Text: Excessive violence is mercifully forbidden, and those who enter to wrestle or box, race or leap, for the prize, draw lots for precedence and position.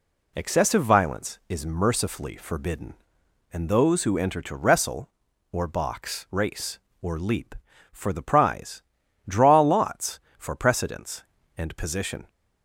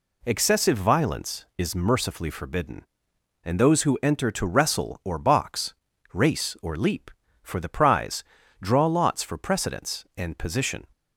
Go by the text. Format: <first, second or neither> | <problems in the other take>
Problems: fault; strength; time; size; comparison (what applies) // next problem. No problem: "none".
neither | none